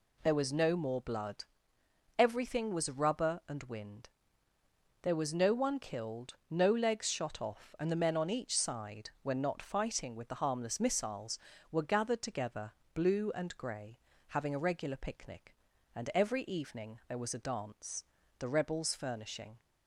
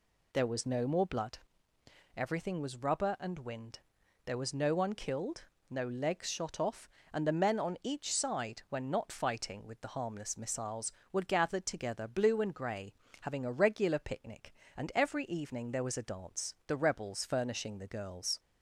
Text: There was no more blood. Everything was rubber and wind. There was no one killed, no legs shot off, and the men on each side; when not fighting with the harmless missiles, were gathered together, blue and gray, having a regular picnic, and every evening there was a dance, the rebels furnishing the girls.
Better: second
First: stops before "the girls"; at 19.5 s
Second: none

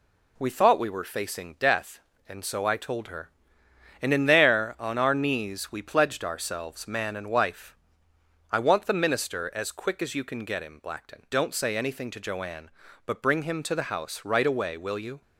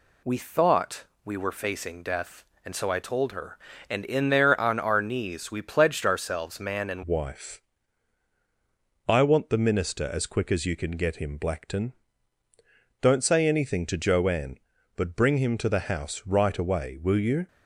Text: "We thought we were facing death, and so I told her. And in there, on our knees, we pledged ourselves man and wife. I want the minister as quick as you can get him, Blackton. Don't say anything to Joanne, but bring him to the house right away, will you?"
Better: first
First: none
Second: pauses between "thought" and "we"; slight; at 1.0 s; 0.22 s long // changes voice at "wife"; from 7.0 s on; 10.4 s long

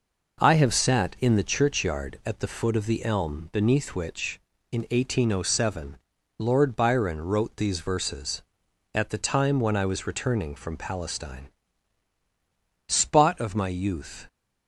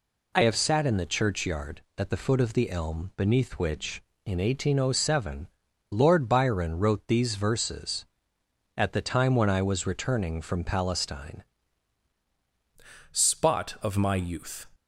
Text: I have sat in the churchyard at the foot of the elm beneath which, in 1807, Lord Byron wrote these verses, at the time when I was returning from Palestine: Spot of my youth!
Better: first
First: none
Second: changes voice at "Spot"; from 13.1 s on; 1.6 s long

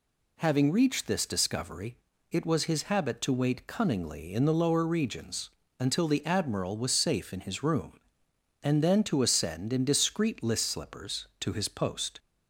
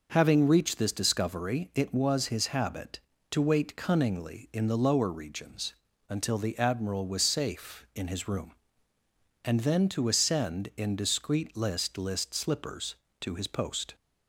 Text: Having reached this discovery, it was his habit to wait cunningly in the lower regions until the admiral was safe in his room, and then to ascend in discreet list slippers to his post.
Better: first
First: pauses between "regions" and "until"; slight; at 5.5 s; 0.28 s long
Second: pauses between "regions" and "until"; slight; at 5.7 s; 0.36 s long // says "list" twice; at 11.9 s

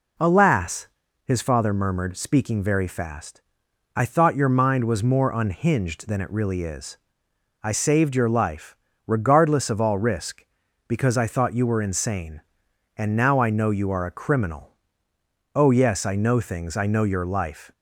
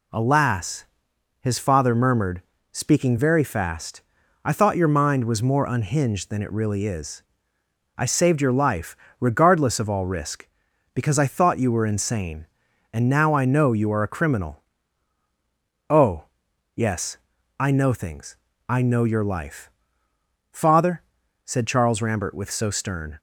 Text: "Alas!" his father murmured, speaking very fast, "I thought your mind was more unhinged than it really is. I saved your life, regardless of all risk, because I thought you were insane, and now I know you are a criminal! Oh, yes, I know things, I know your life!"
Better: first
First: none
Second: goes on to say "Father said Charles Rambert with so stern"; strong; from 20.5 s on; 2.6 s long

